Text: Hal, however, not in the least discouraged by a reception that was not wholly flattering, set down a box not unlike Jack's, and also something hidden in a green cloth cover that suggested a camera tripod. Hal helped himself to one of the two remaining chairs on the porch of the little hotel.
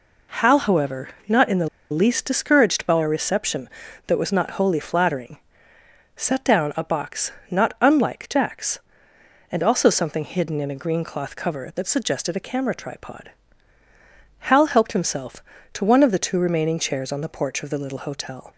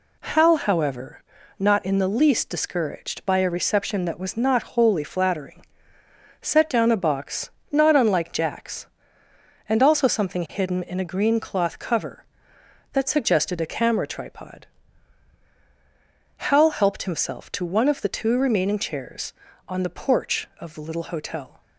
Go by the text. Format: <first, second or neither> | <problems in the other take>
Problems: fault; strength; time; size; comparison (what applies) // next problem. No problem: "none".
second | pauses between "the" and "least"; slight; at 1.6 s; 0.22 s long // pauses between "box" and "not"; slight; at 7.3 s; 0.18 s long; slight in the second